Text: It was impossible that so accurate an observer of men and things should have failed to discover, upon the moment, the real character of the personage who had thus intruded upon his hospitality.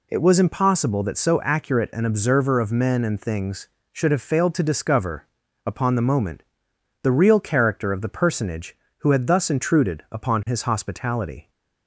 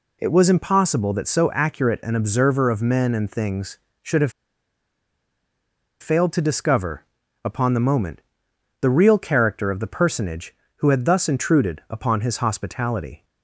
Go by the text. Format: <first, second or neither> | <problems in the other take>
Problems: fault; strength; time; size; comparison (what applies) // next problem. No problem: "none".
first | pauses between "have" and "failed"; strong; at 4.3 s; 1.6 s long